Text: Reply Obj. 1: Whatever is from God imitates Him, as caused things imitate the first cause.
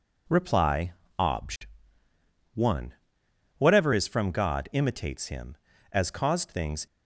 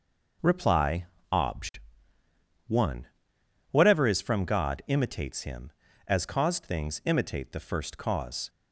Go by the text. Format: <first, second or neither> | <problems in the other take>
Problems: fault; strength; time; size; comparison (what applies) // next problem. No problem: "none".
second | pauses between "Reply" and "Obj"; slight; at 0.9 s; 0.26 s long; slight in the second // stops before "imitate the first cause"; at 6.8 s